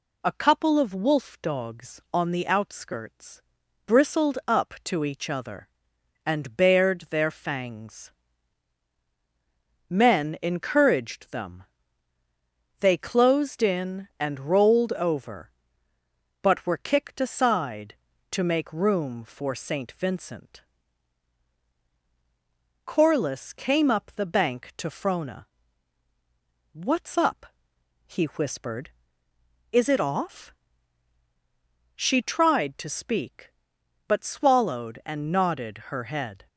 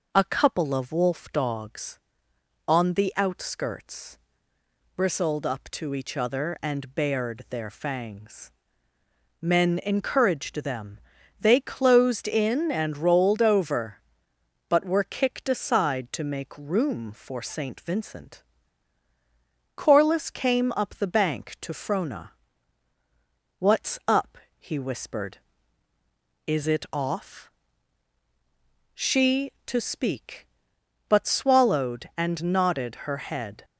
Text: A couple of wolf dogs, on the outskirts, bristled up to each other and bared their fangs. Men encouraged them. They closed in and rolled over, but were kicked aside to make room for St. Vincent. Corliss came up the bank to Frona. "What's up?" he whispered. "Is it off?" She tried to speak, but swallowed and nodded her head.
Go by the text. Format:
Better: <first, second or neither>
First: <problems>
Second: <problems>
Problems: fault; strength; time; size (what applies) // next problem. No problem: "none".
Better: first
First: none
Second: skips "tried"; at 29.5 s